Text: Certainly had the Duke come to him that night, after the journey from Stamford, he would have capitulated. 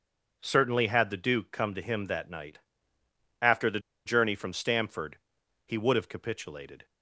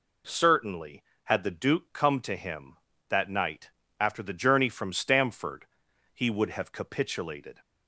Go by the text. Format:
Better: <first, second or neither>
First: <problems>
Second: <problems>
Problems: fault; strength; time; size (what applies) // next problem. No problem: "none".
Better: second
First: pauses between "the" and "journey"; slight; at 3.8 s; 0.25 s long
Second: none